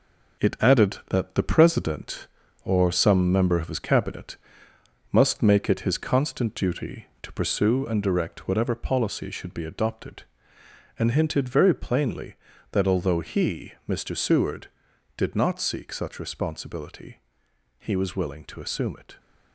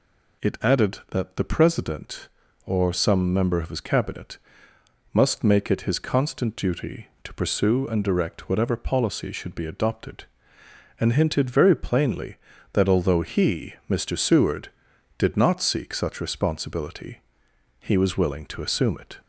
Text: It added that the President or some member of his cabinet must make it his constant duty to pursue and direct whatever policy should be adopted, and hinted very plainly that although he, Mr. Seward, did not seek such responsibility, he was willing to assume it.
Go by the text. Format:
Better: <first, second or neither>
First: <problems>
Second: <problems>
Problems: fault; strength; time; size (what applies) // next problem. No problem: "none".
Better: second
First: gets quieter; noticeable; throughout; 6 dB // pauses between "cabinet" and "must"; noticeable; at 4.3 s; 0.74 s long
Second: pauses between "cabinet" and "must"; noticeable; at 4.3 s; 0.74 s long